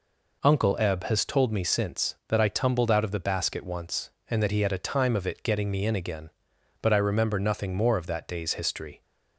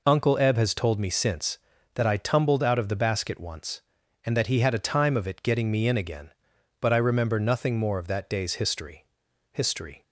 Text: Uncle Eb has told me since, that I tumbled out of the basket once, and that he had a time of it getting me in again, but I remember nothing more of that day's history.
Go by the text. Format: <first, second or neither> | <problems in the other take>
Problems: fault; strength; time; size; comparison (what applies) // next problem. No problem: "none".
first | says "history" twice; at 9.5 s